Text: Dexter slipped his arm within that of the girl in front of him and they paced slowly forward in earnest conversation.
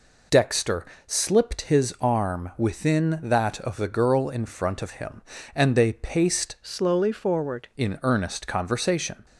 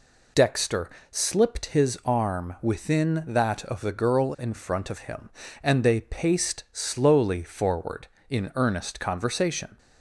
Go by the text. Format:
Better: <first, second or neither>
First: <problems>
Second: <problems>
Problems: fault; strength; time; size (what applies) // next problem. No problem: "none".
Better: second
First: pauses between "Dexter" and "slipped"; slight; at 0.8 s; 0.22 s long // changes voice from "slowly" to "forward"; from 6.6 to 7.6 s; 1.0 s long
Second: pauses between "Dexter" and "slipped"; slight; at 0.8 s; 0.22 s long